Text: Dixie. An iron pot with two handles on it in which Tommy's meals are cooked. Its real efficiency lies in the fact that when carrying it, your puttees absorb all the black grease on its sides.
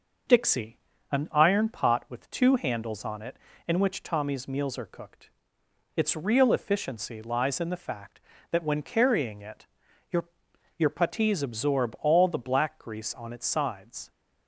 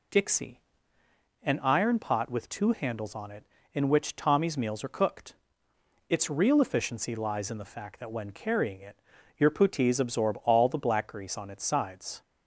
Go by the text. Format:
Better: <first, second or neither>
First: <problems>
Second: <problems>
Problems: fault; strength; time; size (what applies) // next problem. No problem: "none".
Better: second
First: says "your" twice; at 10.7 s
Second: none